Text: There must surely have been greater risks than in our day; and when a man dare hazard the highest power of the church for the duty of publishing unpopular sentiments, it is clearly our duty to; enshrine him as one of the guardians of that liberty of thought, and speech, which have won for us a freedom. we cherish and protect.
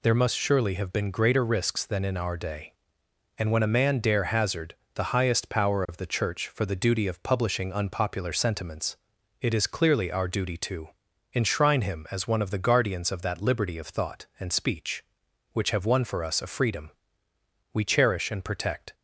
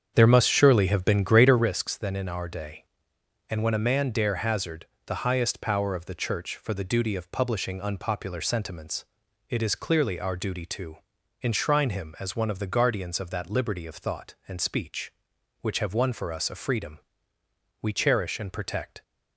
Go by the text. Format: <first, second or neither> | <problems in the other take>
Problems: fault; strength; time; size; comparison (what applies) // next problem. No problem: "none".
first | starts louder than the rest; strong; until 1.7 s; 7.5 dB // pauses between "hazard" and "the"; slight; at 4.8 s; 0.18 s long; slight in the first